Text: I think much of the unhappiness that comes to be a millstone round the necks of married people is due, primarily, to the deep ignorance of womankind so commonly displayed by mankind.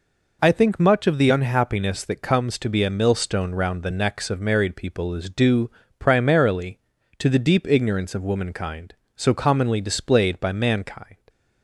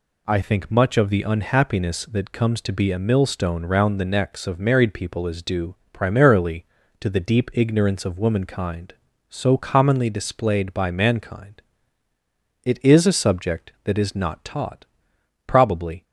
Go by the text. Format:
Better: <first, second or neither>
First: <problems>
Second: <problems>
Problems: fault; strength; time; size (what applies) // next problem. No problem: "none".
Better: first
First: none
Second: goes on to say "It is a subject that is not taught probably"; strong; from 12.6 s on; 3.3 s long